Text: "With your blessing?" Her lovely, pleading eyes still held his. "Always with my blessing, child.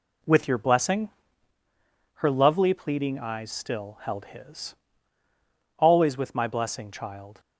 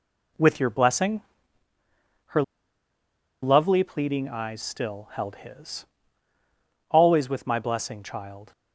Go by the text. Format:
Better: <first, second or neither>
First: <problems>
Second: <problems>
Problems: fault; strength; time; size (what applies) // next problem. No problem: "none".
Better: first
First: none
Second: pauses between "Her" and "lovely"; at 2.4 s; 1.0 s long